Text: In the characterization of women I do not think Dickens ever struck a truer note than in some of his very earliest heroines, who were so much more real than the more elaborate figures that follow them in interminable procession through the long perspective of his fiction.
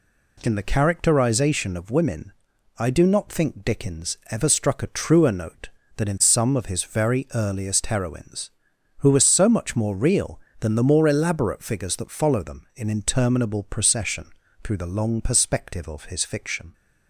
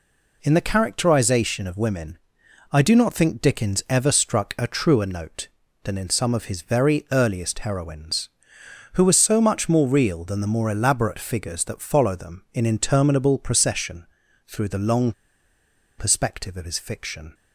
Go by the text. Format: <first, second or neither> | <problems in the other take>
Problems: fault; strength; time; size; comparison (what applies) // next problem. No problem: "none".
first | pauses between "women" and "I"; noticeable; at 2.1 s; 0.54 s long; noticeable in the first // pauses between "procession" and "through"; at 14.0 s; 0.42 s long; slight in the first // pauses between "long" and "perspective"; noticeable; at 15.1 s; 0.86 s long